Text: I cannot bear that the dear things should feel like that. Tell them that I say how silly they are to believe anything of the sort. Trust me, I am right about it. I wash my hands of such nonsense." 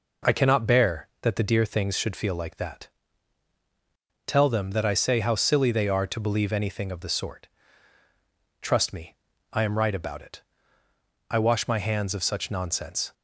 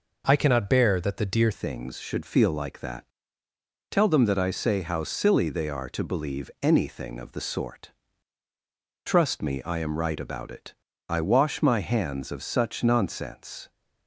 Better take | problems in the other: first | changes voice at "things"; from 1.5 s on; 12.1 s long

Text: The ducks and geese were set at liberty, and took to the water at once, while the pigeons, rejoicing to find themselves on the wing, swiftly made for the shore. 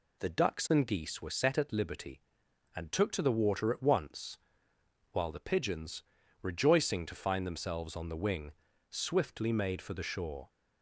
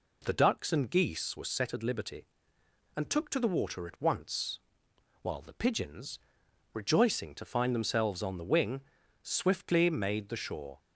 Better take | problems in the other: first | skips "for"; at 10.2 s

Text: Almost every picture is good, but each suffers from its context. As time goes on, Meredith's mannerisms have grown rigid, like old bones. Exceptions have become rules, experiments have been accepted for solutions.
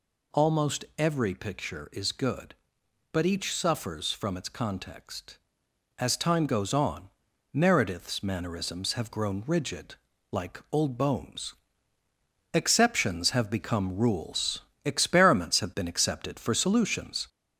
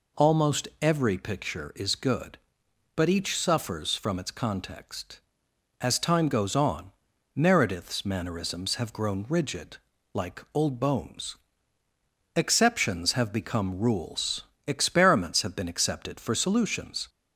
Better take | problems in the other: second | gets louder; slight; throughout; 3 dB

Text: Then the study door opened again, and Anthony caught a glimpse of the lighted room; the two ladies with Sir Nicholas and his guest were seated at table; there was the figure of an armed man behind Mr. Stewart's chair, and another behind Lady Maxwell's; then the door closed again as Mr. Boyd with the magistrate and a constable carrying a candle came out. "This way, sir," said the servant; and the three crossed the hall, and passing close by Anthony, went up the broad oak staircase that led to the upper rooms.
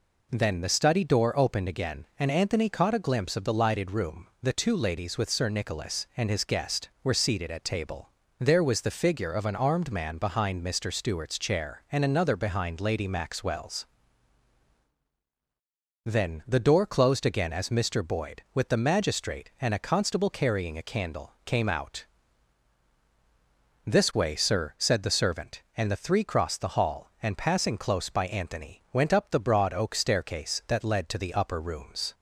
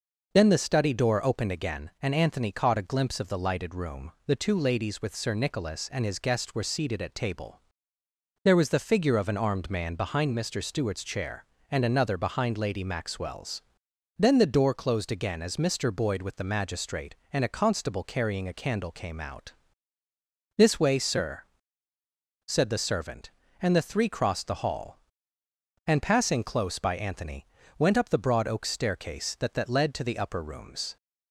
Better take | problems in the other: first | says "that" twice; at 29.5 s

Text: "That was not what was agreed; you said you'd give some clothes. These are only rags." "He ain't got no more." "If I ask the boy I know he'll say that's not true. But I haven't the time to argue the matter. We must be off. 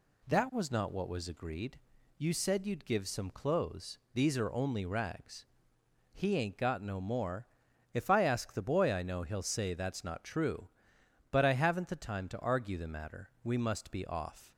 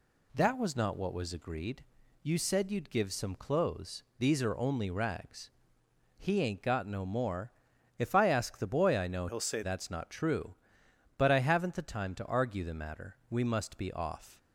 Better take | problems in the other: first | changes voice from "he'll" to "say"; from 9.2 to 9.6 s; 0.4 s long

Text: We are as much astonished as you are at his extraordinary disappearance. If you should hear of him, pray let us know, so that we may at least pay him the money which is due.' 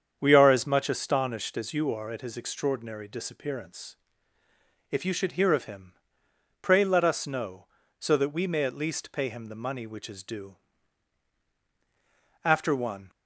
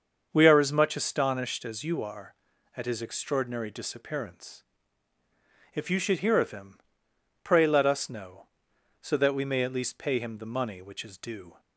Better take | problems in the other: second | starts louder than the rest; strong; until 1.2 s; 7.5 dB; also in the second // goes on to say "After one"; noticeable; from 12.4 s on; 0.66 s long

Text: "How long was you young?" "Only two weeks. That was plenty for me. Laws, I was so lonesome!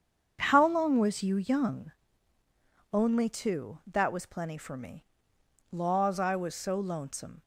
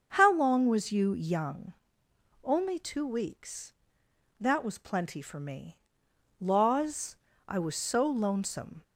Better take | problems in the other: second | starts louder than the rest; strong; until 1.4 s; 7.5 dB; also in the second // skips "weeks"; at 3.8 s

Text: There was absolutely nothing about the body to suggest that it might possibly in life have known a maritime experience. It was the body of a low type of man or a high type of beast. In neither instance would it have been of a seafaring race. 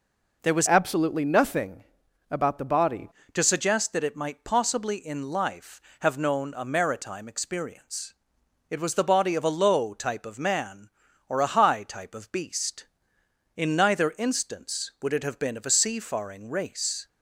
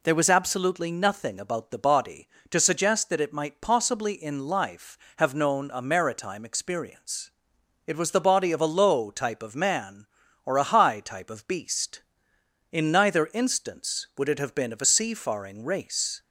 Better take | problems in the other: second | changes voice from "absolutely" to "body"; from 0.6 to 3.0 s; 2.4 s long // pauses between "nothing" and "about"; noticeable; at 1.8 s; 0.48 s long

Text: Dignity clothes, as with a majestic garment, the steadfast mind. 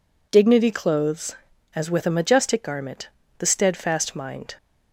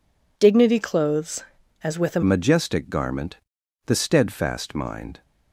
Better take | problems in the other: first | changes voice at "majestic"; from 2.2 s on; 3.0 s long

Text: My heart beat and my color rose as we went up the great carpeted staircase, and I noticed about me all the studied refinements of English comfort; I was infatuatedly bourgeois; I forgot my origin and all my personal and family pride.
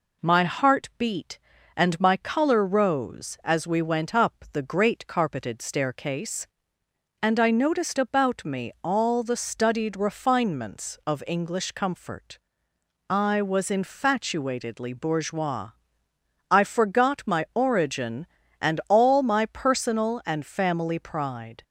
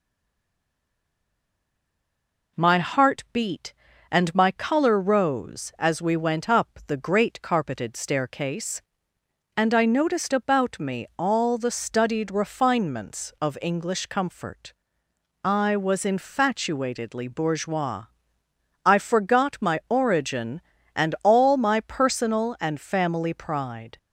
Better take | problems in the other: first | stays silent before the first word; strong; until 2.5 s; 2.5 s long

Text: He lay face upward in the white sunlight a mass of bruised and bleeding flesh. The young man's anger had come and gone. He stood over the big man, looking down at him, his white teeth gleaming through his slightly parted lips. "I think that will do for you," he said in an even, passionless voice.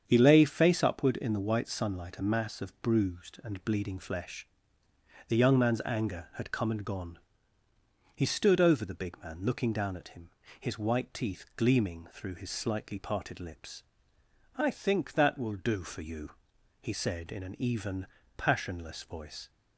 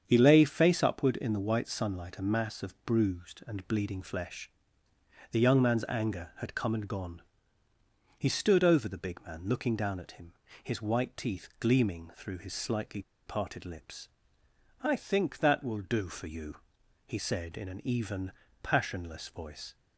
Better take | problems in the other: first | starts louder than the rest; strong; until 1.0 s; 7.5 dB; strong in the first // pauses between "slightly" and "parted"; slight; at 13.0 s; 0.25 s long

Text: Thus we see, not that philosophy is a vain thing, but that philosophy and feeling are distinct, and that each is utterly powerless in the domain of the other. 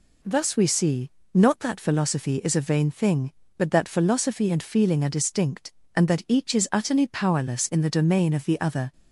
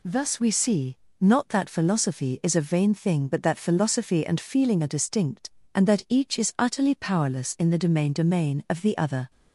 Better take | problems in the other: first | says "domain" twice; at 8.1 s

